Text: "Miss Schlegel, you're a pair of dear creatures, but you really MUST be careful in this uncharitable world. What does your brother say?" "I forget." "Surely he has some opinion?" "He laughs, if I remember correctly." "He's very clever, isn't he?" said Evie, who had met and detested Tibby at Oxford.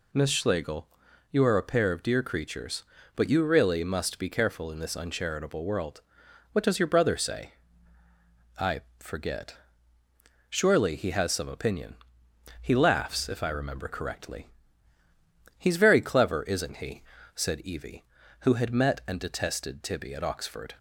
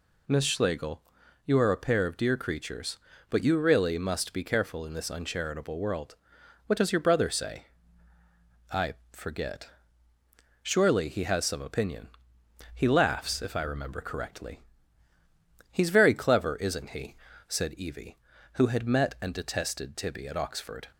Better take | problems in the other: neither | pauses between "I" and "forget"; slight; the same in both

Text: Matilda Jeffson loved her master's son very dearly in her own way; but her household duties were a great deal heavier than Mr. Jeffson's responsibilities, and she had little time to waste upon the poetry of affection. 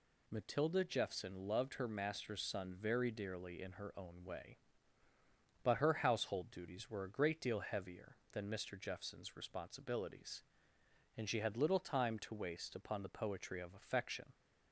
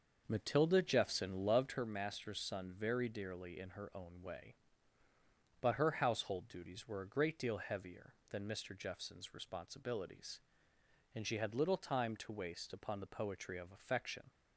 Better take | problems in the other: first | starts louder than the rest; noticeable; until 1.9 s; 6 dB

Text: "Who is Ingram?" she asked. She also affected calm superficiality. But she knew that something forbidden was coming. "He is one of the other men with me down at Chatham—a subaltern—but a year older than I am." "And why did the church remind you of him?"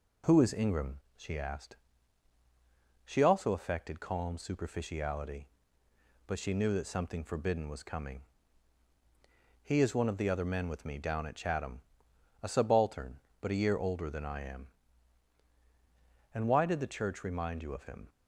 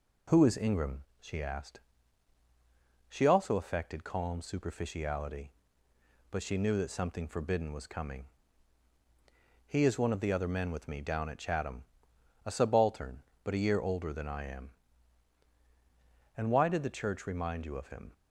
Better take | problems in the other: neither | none

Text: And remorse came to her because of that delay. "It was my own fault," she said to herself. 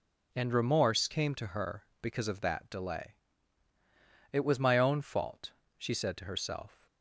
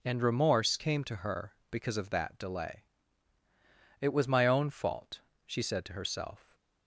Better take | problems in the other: neither | none

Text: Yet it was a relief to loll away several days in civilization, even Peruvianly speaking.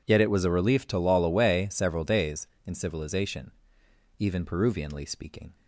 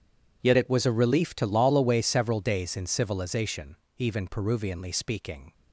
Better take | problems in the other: first | changes voice at "it"; from 0.5 s on; 5.0 s long

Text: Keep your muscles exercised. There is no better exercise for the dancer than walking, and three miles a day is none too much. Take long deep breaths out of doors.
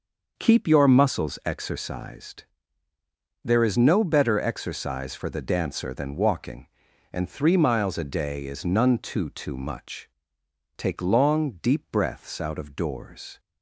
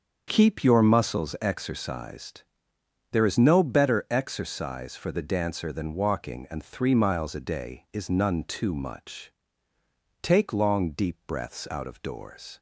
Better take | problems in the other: second | starts louder than the rest; noticeable; until 1.3 s; 6 dB; also in the second // says "too" twice; at 9.2 s

